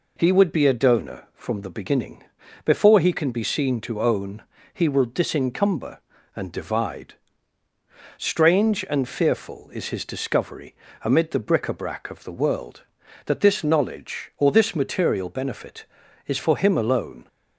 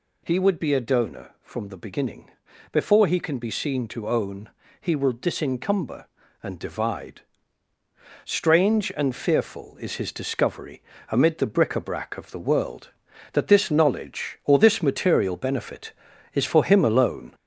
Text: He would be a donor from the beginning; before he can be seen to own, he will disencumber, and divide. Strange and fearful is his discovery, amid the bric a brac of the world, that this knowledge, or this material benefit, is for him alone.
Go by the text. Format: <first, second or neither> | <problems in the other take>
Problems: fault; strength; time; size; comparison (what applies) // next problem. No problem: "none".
first | gets louder; noticeable; throughout; 4.5 dB